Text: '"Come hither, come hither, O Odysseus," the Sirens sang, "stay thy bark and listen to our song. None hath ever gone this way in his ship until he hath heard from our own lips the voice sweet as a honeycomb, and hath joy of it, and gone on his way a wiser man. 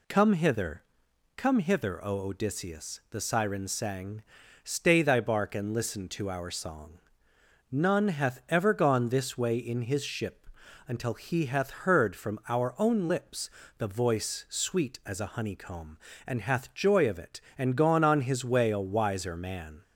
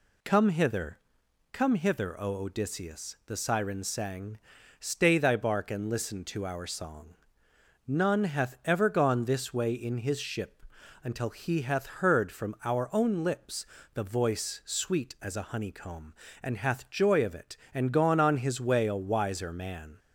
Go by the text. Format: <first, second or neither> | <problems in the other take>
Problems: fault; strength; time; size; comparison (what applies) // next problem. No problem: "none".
neither | pauses between "ship" and "until"; the same in both // pauses between "lips" and "the"; slight; the same in both